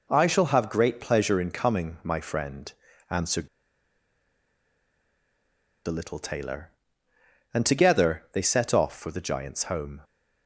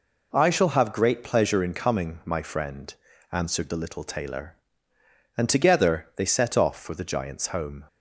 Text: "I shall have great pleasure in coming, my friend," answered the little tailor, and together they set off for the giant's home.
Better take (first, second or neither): second